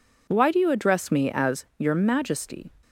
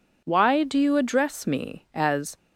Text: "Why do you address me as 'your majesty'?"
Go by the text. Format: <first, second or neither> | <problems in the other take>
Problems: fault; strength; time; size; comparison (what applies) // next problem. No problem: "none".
first | stops before "your majesty"; at 2.3 s